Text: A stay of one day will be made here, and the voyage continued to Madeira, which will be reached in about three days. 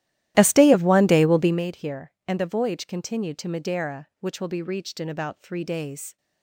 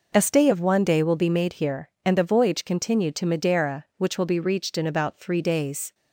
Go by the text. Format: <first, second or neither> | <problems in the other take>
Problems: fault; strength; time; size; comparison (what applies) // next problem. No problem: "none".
second | starts louder than the rest; strong; until 1.6 s; 14 dB